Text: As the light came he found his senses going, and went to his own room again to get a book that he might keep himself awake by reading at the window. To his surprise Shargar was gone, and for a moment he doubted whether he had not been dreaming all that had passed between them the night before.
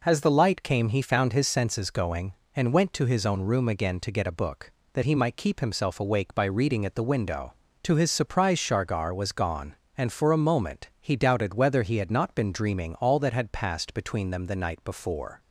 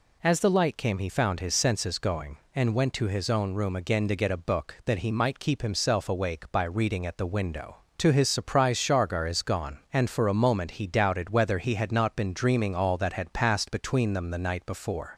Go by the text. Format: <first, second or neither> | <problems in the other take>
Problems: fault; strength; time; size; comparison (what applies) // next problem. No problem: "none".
first | says "is" for "was"; at 9.2 s